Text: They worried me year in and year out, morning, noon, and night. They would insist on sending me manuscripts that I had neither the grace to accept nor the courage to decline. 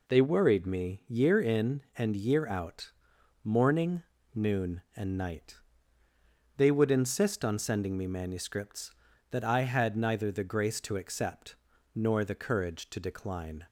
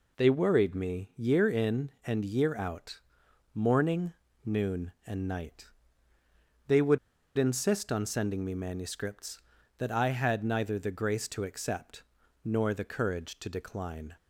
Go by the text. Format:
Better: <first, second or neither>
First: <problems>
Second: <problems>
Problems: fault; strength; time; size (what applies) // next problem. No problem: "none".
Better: first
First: pauses between "accept" and "nor"; at 11.5 s; 0.40 s long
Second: pauses between "would" and "insist"; at 6.9 s; 0.39 s long // pauses between "accept" and "nor"; at 12.0 s; 0.42 s long